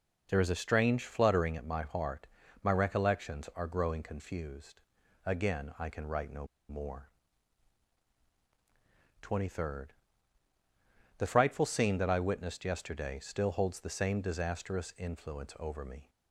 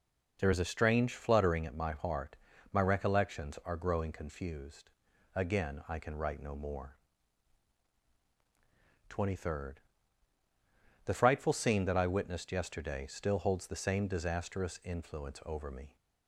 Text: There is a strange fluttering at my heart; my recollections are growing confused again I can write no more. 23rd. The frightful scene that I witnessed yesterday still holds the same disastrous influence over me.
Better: second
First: pauses between "confused" and "again"; at 4.8 s; 0.42 s long // pauses between "no" and "more"; slight; at 6.4 s; 0.24 s long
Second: pauses between "confused" and "again"; at 4.9 s; 0.42 s long

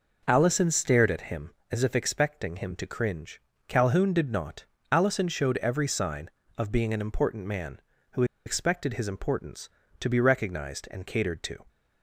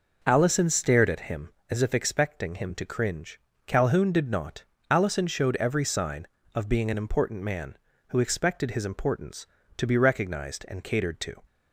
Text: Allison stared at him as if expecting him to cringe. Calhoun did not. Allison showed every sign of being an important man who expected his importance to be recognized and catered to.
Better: second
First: pauses between "who" and "expected"; slight; at 8.2 s; 0.22 s long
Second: none

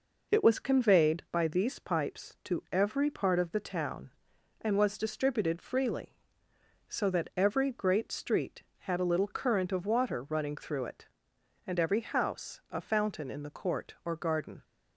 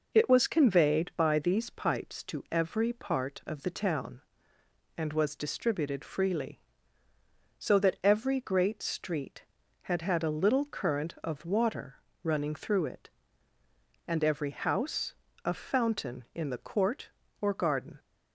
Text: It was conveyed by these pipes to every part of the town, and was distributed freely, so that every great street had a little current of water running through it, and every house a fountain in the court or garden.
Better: first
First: none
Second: says "had" twice; at 10.0 s // pauses between "water" and "running"; slight; at 11.9 s; 0.28 s long // pauses between "house" and "a"; slight; at 15.1 s; 0.30 s long

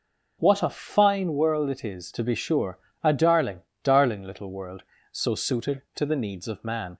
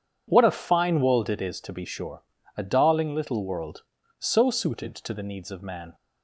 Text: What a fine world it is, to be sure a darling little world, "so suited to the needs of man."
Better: second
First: pauses between "sure" and "a"; slight; at 2.7 s; 0.26 s long // says "darling" twice; at 3.8 s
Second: pauses between "sure" and "a"; slight; at 2.2 s; 0.34 s long

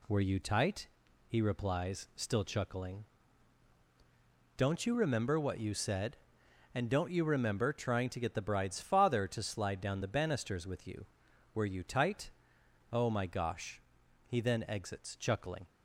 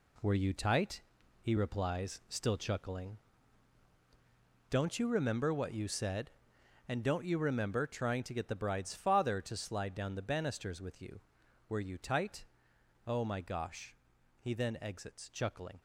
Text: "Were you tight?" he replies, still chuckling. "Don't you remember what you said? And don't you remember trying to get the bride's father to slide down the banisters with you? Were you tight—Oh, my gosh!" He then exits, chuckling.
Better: first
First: none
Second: gets quieter; strong; throughout; 8 dB

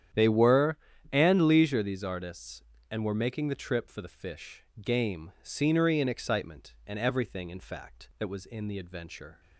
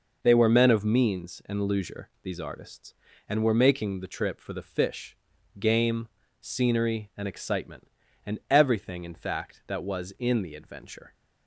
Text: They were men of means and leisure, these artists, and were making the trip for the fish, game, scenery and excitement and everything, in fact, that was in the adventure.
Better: second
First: starts louder than the rest; strong; until 1.5 s; 10 dB // skips "men of means"; at 0.9 s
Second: none

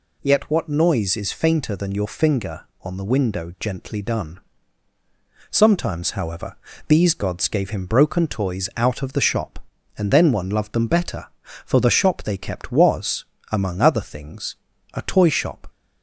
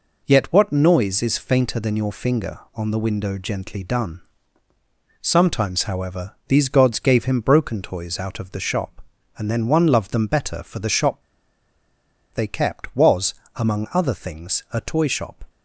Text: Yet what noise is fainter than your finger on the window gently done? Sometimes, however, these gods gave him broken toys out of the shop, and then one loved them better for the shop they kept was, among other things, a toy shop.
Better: first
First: none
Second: pauses between "shop" and "they"; at 11.2 s; 1.1 s long

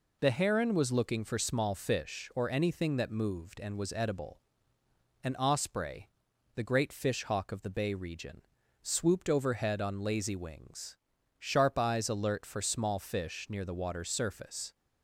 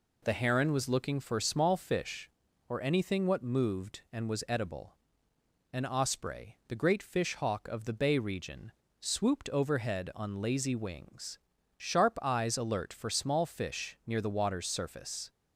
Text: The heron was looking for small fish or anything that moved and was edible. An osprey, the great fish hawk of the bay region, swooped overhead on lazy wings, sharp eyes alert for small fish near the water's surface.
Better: first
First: none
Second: says "what" for "that"; at 3.2 s

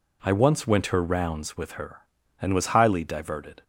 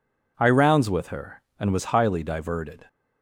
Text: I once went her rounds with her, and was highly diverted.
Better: first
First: none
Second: skips "once went her"; at 0.4 s

